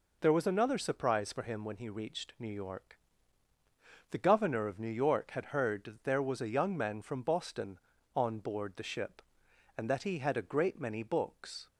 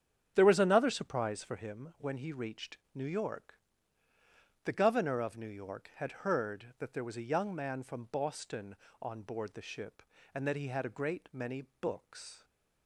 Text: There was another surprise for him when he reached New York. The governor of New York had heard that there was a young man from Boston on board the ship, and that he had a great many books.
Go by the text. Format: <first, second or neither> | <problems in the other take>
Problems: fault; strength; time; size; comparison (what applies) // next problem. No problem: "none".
first | starts louder than the rest; strong; until 1.8 s; 8.5 dB // pauses between "reached" and "New"; slight; at 2.7 s; 0.18 s long // pauses between "many" and "books"; slight; at 11.6 s; 0.16 s long